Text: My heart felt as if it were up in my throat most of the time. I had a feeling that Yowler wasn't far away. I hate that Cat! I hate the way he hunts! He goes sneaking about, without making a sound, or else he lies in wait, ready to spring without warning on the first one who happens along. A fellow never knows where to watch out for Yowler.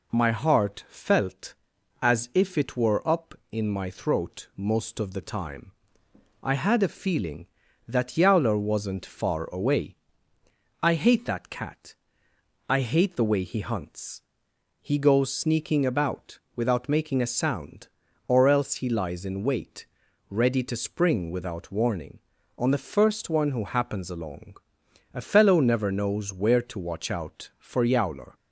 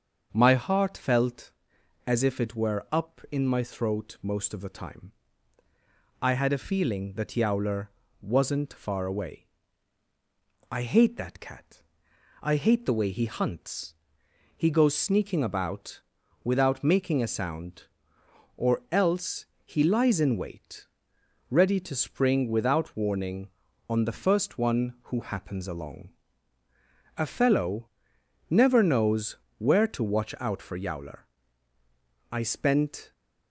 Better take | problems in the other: first | starts louder than the rest; until 1.3 s; 7 dB // pauses between "Yowler" and "wasn't"; slight; at 7.8 s; 0.30 s long // pauses between "else" and "he"; slight; at 19.4 s; 0.18 s long // pauses between "fellow" and "never"; noticeable; at 27.8 s; 0.62 s long // pauses between "knows" and "where"; slight; at 29.3 s; 0.22 s long // goes on to say "I spent"; noticeable; from 32.2 s on; 0.82 s long

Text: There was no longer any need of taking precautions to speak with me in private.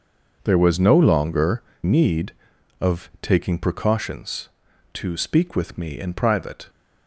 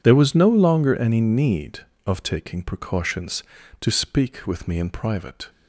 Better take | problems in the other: second | skips "any"; at 1.7 s

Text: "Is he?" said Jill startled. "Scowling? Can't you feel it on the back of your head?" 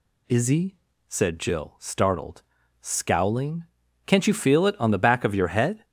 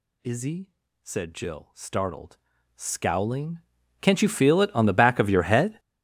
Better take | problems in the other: first | gets louder; strong; throughout; 19 dB

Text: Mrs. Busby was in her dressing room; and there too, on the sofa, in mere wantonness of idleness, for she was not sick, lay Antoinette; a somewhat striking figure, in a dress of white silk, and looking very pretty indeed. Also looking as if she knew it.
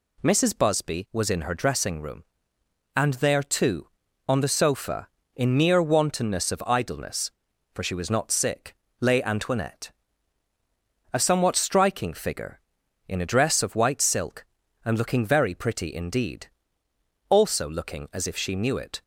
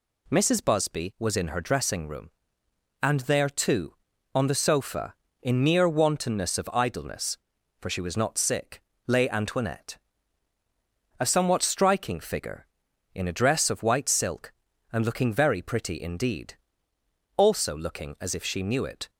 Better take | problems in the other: neither | none

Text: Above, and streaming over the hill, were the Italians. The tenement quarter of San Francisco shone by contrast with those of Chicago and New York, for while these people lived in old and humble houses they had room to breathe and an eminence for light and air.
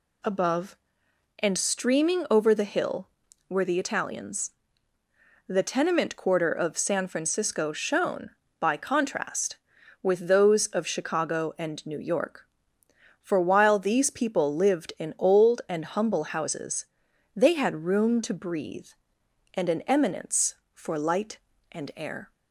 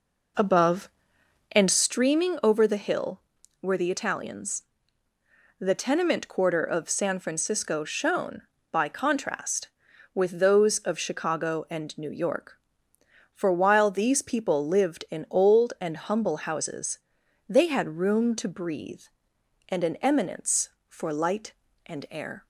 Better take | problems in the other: first | starts louder than the rest; noticeable; until 2.1 s; 4.5 dB // pauses between "houses" and "they"; noticeable; at 16.9 s; 0.50 s long; noticeable in the first

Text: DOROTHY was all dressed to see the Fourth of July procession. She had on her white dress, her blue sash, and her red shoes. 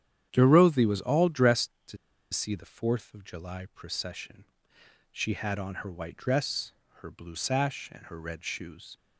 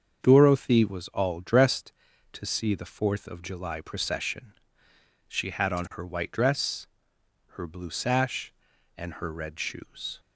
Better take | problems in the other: second | starts louder than the rest; strong; until 1.3 s; 9.5 dB; also in the second // pauses between "to" and "see"; slight; at 1.9 s; 0.35 s long

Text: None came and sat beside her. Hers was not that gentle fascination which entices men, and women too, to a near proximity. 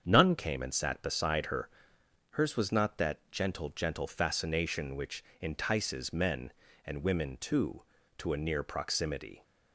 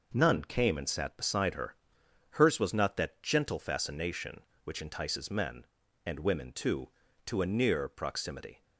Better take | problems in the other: second | starts louder than the rest; strong; until 1.0 s; 7.5 dB // says "gentle" twice; at 3.6 s // pauses between "which" and "entices"; slight; at 5.2 s; 0.18 s long

